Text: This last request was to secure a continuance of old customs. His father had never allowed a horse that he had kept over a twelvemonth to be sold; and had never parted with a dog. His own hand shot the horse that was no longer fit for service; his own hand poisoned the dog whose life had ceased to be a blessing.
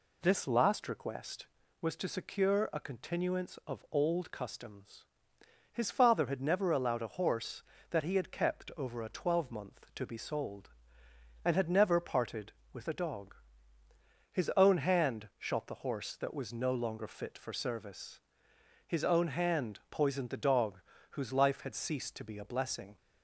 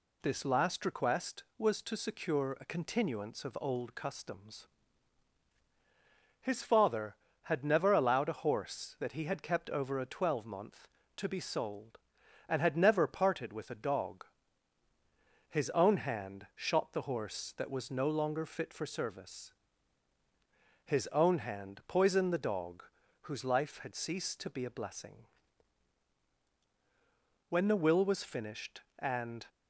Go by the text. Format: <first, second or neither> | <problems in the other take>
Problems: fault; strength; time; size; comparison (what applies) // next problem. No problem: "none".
first | pauses between "dog" and "whose"; at 22.8 s; 0.40 s long; slight in the first // goes on to say "When the will was finished and"; strong; from 27.4 s on; 1.9 s long